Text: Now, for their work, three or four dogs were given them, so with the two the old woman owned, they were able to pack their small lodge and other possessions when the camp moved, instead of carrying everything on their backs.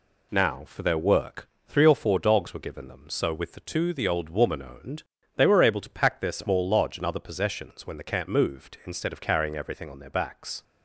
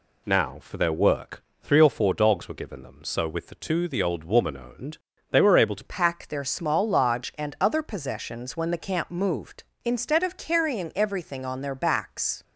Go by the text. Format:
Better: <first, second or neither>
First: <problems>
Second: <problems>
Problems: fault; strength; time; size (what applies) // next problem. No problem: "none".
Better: first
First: none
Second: changes voice at "pack"; from 5.8 s on; 6.6 s long